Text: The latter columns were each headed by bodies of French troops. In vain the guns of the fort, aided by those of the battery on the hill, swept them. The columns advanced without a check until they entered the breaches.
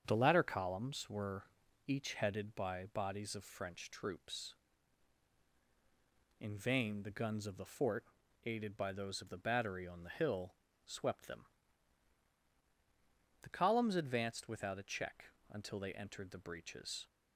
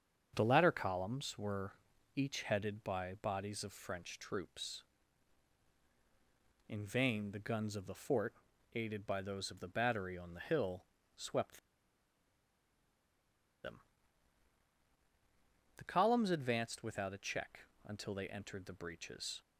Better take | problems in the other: first | starts louder than the rest; strong; until 1.3 s; 7.5 dB; strong in the first // pauses between "were" and "each"; at 1.7 s; 0.42 s long; also in the first // pauses between "swept" and "them"; strong; at 11.5 s; 2.0 s long // pauses between "check" and "until"; slight; at 17.6 s; 0.24 s long; slight in the first

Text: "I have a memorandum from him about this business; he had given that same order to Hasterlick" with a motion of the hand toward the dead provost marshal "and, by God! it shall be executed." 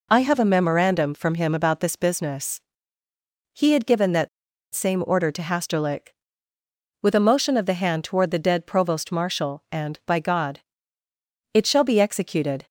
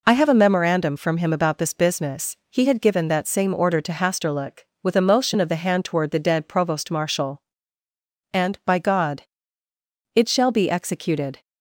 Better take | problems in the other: second | pauses between "that" and "same"; at 4.2 s; 0.45 s long

